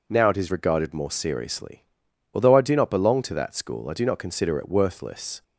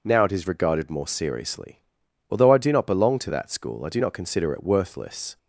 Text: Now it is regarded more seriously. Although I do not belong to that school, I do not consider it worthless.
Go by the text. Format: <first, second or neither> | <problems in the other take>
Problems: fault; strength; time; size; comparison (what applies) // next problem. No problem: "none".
neither | none